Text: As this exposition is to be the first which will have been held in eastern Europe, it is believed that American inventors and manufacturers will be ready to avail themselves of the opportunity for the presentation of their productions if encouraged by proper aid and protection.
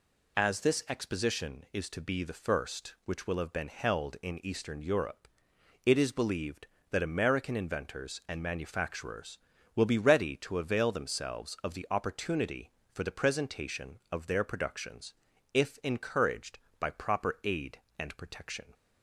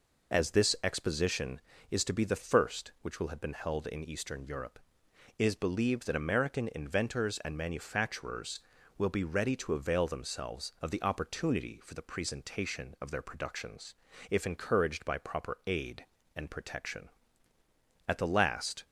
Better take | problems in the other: first | pauses between "productions" and "if"; slight; at 13.9 s; 0.36 s long; also in the first // goes on to say "At the last"; noticeable; from 18.0 s on; 0.78 s long

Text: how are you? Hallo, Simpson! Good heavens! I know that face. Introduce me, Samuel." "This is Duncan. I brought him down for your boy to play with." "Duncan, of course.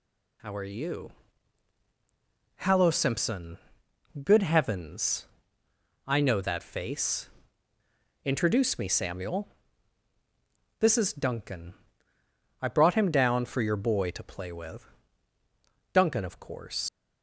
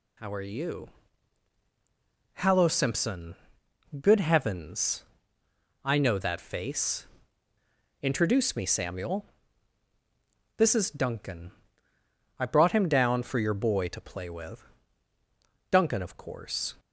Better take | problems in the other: second | leaves "course" unfinished; at 16.8 s; 130 ms

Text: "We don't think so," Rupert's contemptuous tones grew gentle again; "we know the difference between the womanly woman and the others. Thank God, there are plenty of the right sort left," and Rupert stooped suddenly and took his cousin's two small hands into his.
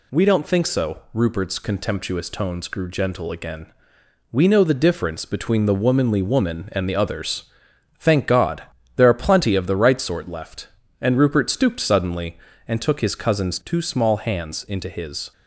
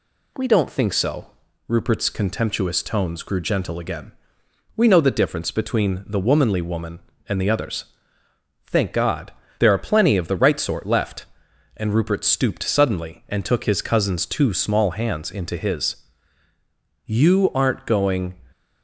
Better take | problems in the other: first | goes on to say "You aren't going"; noticeable; from 17.0 s on; 1.2 s long

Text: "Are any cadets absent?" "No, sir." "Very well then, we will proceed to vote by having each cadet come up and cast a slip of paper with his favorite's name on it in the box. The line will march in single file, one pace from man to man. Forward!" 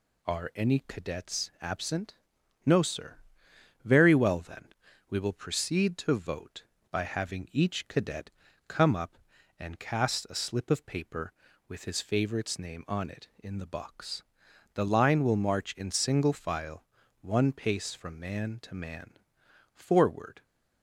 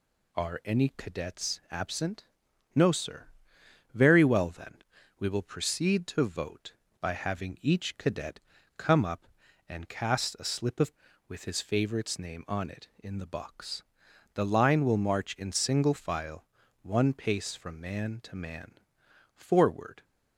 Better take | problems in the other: first | pauses between "cadet" and "come"; at 8.3 s; 0.38 s long; also in the first // skips "paper"; at 11.1 s

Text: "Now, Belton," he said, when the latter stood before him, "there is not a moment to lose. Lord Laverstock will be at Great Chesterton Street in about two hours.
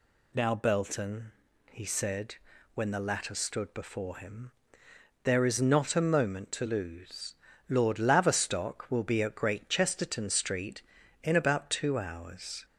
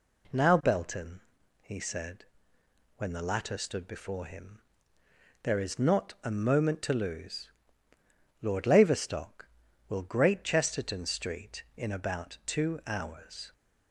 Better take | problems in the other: first | skips "be at"; at 10.0 s

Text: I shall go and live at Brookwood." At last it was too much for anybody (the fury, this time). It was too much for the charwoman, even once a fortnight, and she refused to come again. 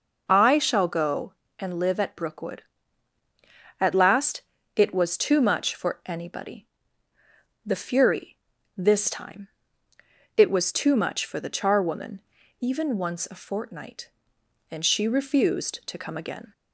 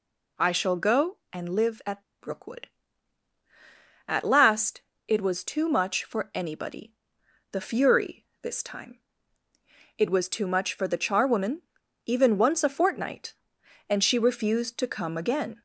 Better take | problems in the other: first | pauses between "at" and "Brookwood"; slight; at 2.0 s; 0.18 s long // pauses between "last" and "it"; slight; at 4.8 s; 0.26 s long; slight in the first

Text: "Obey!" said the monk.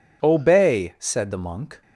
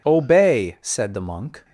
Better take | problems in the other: neither | none

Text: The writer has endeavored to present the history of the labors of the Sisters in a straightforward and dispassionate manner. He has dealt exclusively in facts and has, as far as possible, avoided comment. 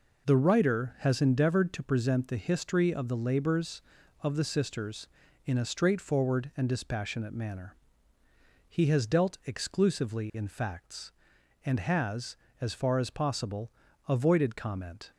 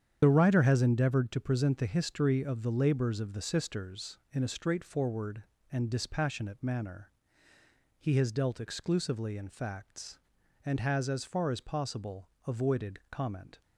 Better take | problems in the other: first | loses the start of "The"; at 0.2 s; 45 ms // starts louder than the rest; strong; until 1.2 s; 8.5 dB

